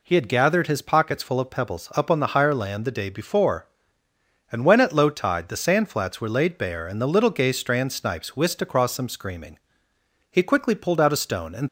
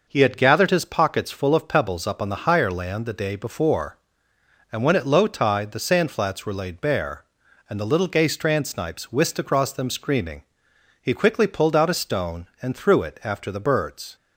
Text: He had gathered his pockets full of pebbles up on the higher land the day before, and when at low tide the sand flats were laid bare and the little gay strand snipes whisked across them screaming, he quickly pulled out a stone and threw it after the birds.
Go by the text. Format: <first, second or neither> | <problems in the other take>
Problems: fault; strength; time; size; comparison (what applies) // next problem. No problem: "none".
second | stops before "threw it after the birds"; at 11.6 s